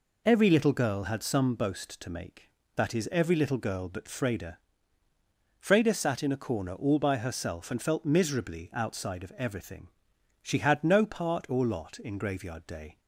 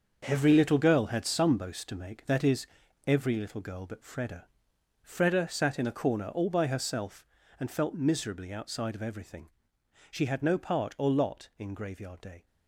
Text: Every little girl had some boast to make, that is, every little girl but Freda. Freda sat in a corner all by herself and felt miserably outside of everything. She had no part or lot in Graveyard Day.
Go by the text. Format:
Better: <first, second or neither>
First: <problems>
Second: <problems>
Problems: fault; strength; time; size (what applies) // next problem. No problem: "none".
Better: first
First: none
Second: gets quieter; strong; throughout; 9.5 dB